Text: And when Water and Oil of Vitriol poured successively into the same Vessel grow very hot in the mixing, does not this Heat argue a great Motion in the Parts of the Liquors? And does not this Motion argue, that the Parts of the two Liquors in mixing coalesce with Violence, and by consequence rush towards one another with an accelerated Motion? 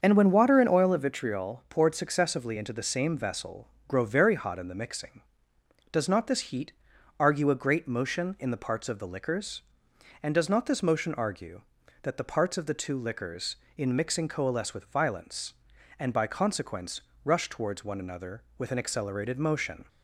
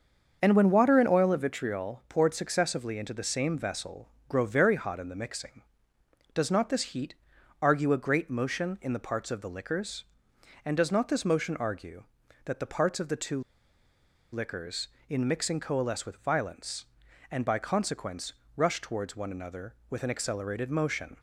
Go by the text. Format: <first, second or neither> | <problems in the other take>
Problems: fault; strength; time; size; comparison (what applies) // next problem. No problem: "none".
first | starts louder than the rest; until 1.4 s; 6.5 dB; also in the first // pauses between "Vessel" and "grow"; slight; at 4.0 s; 0.22 s long; slight in the first // pauses between "Heat" and "argue"; noticeable; at 7.1 s; 0.46 s long; noticeable in the first // pauses between "two" and "Liquors"; noticeable; at 13.3 s; 0.92 s long // pauses between "consequence" and "rush"; slight; at 18.3 s; 0.22 s long; slight in the first